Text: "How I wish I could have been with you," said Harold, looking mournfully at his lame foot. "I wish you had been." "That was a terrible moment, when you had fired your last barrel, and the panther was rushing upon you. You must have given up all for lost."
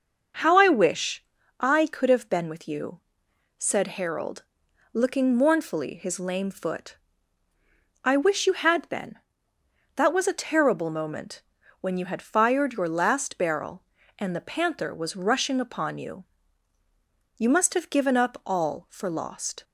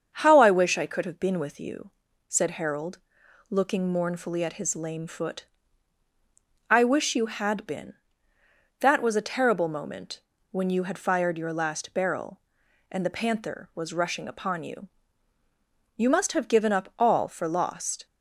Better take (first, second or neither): second